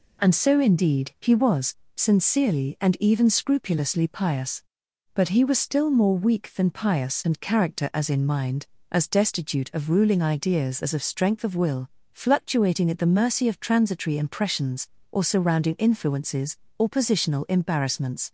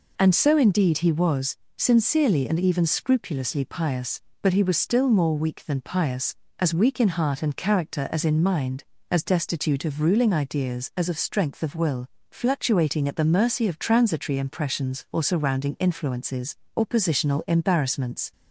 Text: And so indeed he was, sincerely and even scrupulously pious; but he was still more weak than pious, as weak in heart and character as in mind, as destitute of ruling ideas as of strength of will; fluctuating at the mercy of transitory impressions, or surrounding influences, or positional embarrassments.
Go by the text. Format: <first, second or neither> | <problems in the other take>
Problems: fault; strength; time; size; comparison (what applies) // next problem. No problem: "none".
second | skips "as weak in heart"; at 7.2 s